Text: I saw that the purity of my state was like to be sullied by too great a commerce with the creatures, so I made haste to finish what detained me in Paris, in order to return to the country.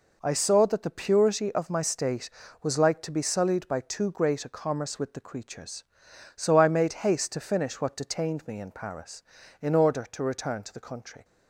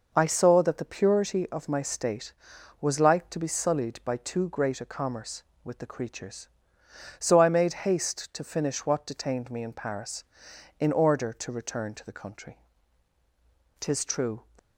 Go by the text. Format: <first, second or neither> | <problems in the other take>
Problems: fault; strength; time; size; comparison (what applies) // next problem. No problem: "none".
first | goes on to say "Tis true"; noticeable; from 13.8 s on; 0.64 s long